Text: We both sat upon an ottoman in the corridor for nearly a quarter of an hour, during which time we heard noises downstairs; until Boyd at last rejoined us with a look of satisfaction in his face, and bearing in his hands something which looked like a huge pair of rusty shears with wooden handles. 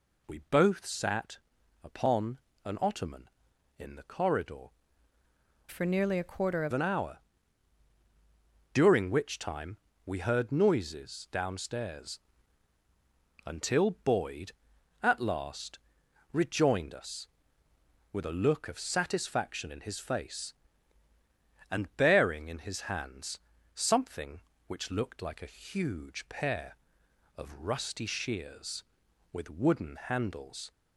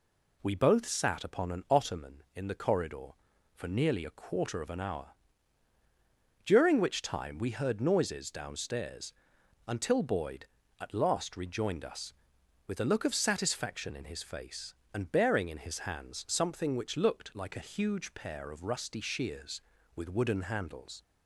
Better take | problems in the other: second | pauses between "sat" and "upon"; at 1.3 s; 0.44 s long // pauses between "upon" and "an"; slight; at 2.3 s; 0.26 s long // changes voice from "for" to "of"; from 5.6 to 6.7 s; 1.1 s long // pauses between "time" and "we"; slight; at 9.7 s; 0.28 s long // pauses between "last" and "rejoined"; noticeable; at 15.7 s; 0.54 s long // pauses between "hands" and "something"; slight; at 23.3 s; 0.36 s long

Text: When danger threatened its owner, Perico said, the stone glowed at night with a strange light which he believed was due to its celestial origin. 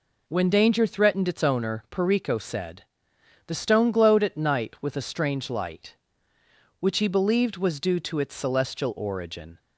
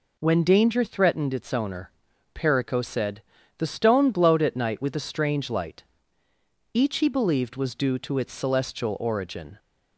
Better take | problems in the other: first | says "each" for "which"; at 6.7 s

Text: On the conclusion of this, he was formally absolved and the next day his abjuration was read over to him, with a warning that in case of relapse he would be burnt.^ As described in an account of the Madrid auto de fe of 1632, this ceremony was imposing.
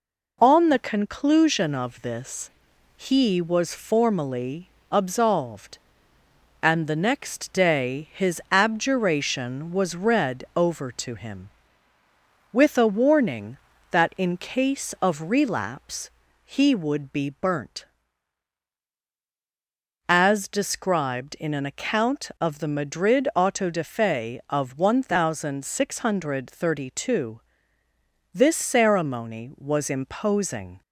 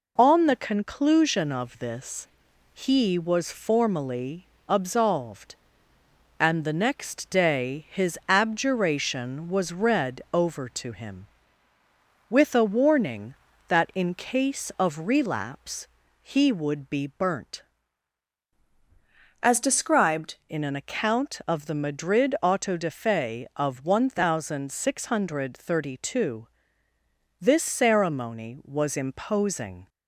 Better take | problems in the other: first | pauses between "formally" and "absolved"; slight; at 4.4 s; 0.20 s long; slight in the first // pauses between "relapse" and "he"; slight; at 15.8 s; 0.34 s long; slight in the first // changes voice from "As" to "described"; from 19.4 to 20.3 s; 0.9 s long

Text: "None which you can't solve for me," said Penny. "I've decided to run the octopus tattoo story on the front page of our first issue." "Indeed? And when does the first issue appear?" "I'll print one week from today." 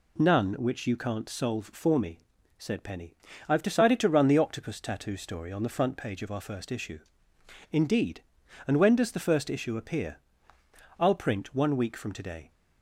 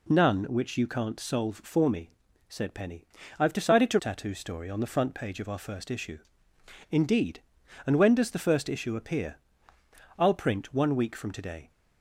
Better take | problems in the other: first | skips "run the octopus"; at 3.9 s

